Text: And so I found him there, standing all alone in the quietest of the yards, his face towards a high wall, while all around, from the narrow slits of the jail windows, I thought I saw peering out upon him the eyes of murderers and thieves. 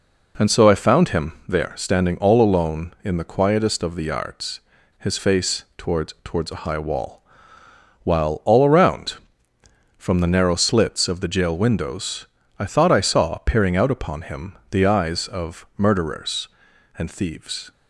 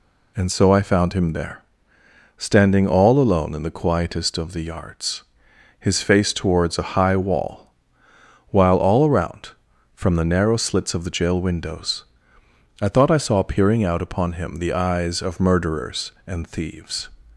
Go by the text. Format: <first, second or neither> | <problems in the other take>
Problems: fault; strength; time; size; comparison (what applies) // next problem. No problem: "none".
second | pauses between "him" and "there"; slight; at 1.3 s; 0.16 s long // says "towards" twice; at 6.2 s